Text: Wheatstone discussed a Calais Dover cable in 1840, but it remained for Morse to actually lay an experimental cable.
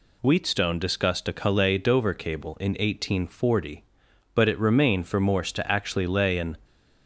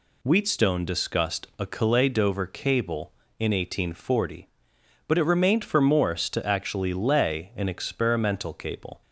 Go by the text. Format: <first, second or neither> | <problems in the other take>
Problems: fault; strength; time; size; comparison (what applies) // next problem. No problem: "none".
second | stops before "experimental cable"; at 6.6 s